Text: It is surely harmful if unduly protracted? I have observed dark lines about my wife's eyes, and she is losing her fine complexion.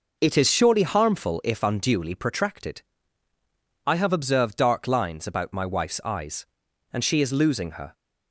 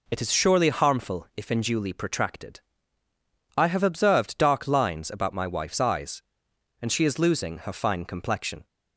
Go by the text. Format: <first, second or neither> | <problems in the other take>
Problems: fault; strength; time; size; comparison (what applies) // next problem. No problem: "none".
second | stops before "fine complexion"; at 7.9 s